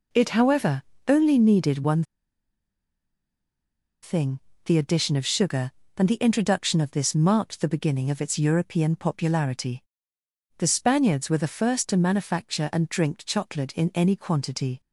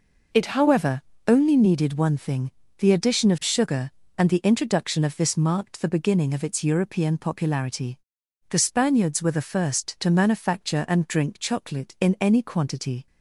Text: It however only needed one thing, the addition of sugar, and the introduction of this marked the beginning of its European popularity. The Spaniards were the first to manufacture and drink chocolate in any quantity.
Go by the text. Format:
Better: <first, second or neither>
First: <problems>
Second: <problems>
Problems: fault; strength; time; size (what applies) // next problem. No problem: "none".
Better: second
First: pauses between "however" and "only"; slight; at 0.8 s; 0.24 s long // pauses between "one" and "thing"; strong; at 2.0 s; 1.9 s long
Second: pauses between "however" and "only"; slight; at 1.0 s; 0.26 s long